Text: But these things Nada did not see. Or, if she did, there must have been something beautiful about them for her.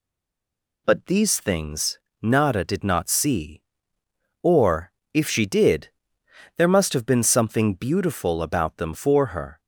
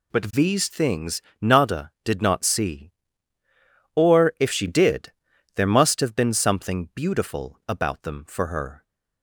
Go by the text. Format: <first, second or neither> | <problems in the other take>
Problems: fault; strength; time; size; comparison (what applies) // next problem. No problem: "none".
second | stays silent before the first word; slight; until 0.8 s; 0.8 s long // pauses between "things" and "Nada"; slight; at 1.9 s; 0.22 s long; slight in the second